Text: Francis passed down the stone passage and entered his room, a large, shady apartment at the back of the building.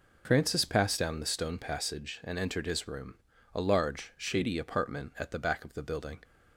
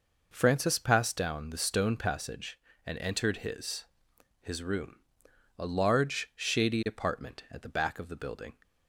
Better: first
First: none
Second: says "his" twice; at 4.4 s

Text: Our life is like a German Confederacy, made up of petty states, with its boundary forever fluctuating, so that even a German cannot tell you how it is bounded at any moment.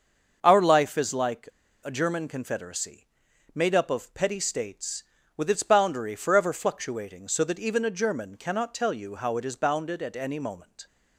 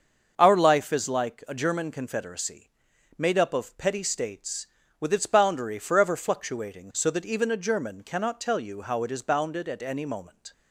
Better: second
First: starts louder than the rest; until 1.4 s; 6.5 dB // pauses between "like" and "a"; slight; at 1.4 s; 0.33 s long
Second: starts louder than the rest; until 1.3 s; 6.5 dB

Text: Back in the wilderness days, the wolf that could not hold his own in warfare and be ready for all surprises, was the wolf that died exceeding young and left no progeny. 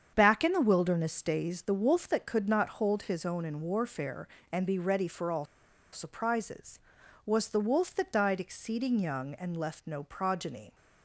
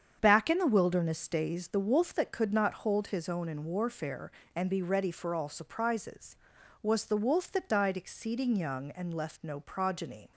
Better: second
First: starts louder than the rest; strong; until 1.1 s; 7.5 dB // pauses between "all" and "surprises"; noticeable; at 5.4 s; 0.48 s long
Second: starts louder than the rest; strong; until 1.2 s; 7.5 dB

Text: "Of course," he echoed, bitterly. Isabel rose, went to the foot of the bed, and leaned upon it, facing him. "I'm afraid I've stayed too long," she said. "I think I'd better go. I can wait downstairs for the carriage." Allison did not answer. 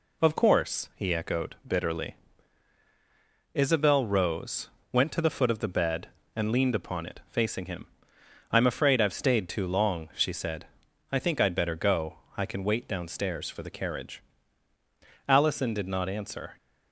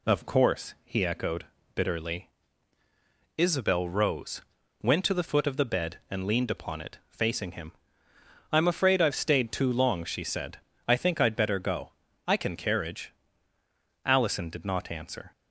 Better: first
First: none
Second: skips "wait downstairs for the"; at 12.5 s

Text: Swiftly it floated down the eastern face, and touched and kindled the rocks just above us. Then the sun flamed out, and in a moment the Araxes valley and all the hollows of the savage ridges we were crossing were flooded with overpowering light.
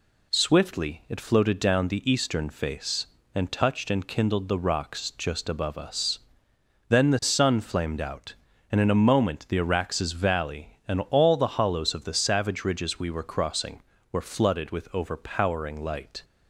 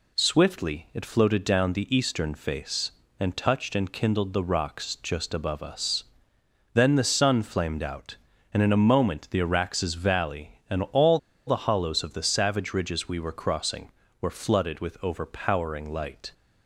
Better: first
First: none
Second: pauses between "all" and "the"; slight; at 11.1 s; 0.29 s long

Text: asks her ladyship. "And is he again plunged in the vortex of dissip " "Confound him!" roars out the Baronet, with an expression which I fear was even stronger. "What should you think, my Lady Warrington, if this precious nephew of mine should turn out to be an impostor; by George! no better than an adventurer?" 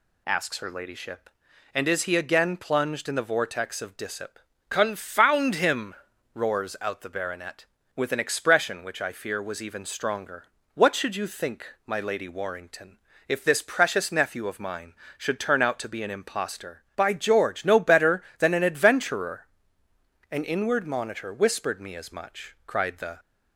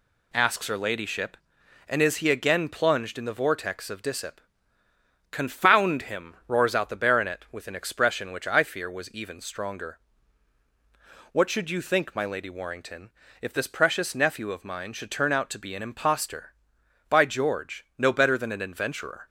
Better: second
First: goes on to say "An inward monitor whispered me as much cried the"; strong; from 20.3 s on; 2.8 s long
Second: none

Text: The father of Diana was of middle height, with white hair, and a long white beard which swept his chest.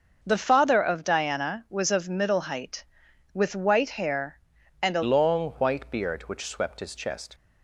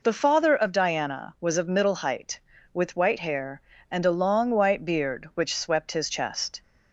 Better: second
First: starts louder than the rest; until 1.2 s; 6 dB // changes voice at "long"; from 5.0 s on; 2.3 s long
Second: none

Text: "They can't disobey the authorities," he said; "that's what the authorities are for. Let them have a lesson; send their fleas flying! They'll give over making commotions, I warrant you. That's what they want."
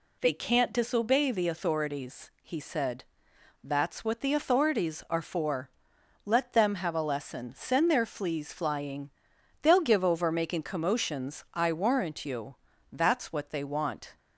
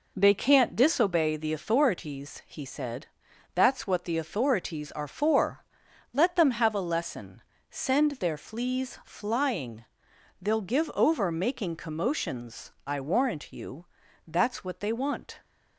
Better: neither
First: none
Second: none

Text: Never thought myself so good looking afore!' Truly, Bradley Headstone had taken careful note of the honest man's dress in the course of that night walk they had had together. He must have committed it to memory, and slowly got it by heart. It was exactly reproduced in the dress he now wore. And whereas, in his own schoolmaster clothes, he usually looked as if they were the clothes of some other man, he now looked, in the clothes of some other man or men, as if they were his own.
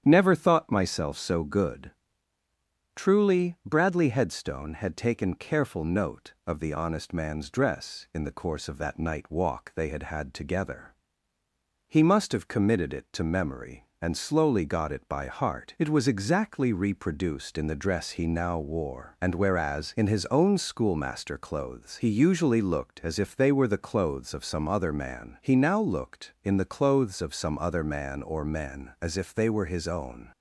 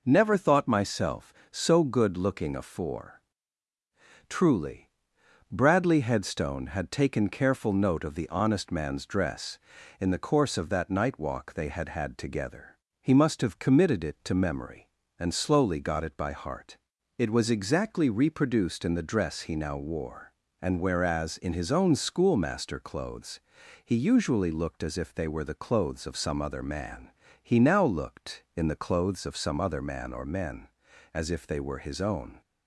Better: second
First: starts louder than the rest; strong; until 1.0 s; 9.5 dB // skips "looking afore"; at 2.4 s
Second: none

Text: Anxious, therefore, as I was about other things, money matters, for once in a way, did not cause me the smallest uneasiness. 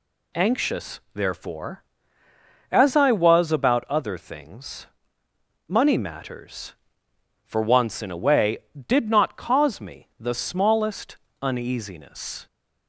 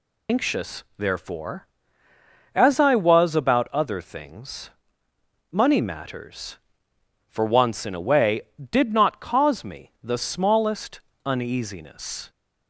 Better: first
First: pauses between "smallest" and "uneasiness"; slight; at 11.1 s; 0.26 s long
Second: loses the start of "Anxious"; at 0.2 s; 115 ms // pauses between "smallest" and "uneasiness"; slight; at 11.0 s; 0.26 s long

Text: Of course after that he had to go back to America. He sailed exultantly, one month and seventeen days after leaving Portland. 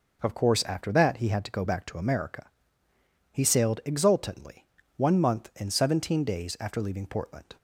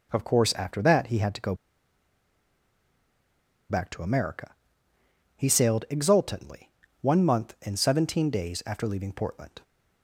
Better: first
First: none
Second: pauses between "go" and "back"; strong; at 1.5 s; 2.1 s long

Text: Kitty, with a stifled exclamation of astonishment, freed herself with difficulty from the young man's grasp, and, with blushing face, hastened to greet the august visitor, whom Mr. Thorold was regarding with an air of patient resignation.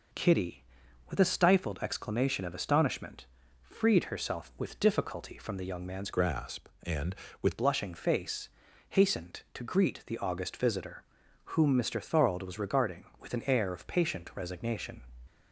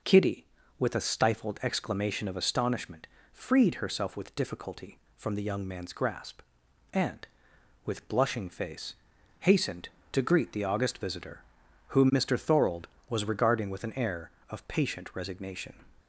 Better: second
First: changes voice from "grasp" to "with"; from 6.1 to 7.5 s; 1.4 s long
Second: none

